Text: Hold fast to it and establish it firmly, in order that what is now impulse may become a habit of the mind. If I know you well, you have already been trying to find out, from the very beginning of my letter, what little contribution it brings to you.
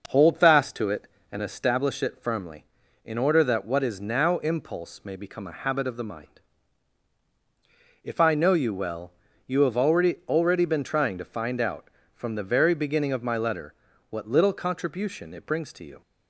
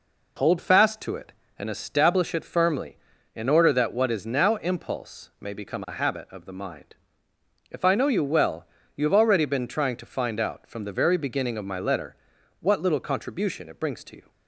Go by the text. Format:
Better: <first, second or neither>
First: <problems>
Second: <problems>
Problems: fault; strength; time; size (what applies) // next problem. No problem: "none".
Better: second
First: says "already" twice; at 10.2 s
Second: none